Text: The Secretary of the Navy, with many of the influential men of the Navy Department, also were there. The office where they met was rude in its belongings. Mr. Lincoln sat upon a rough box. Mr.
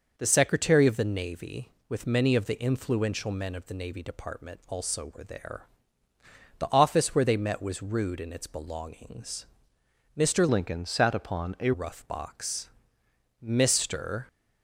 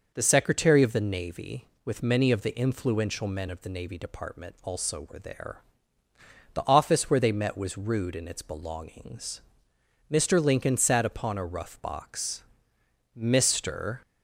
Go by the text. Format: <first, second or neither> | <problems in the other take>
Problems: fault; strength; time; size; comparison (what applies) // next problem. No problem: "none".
second | changes voice from "Lincoln" to "a"; from 10.4 to 11.7 s; 1.3 s long